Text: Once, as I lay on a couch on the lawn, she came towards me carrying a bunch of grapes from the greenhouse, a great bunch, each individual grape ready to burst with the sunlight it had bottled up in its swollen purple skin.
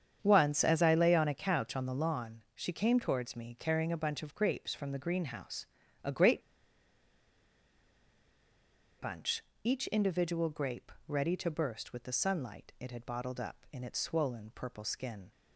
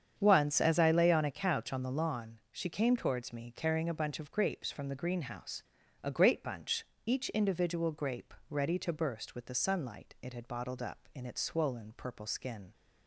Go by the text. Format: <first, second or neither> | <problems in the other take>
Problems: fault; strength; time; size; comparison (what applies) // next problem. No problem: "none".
second | starts louder than the rest; strong; until 1.2 s; 8 dB; strong in the second // pauses between "great" and "bunch"; strong; at 6.4 s; 2.5 s long // pauses between "grape" and "ready"; slight; at 10.9 s; 0.16 s long; slight in the second